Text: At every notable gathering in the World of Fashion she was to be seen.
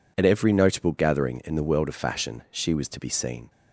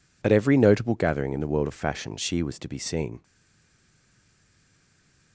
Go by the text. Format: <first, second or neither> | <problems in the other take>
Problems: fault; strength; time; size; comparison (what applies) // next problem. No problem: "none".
first | stays silent after the last word; from 3.2 s on; 2.1 s long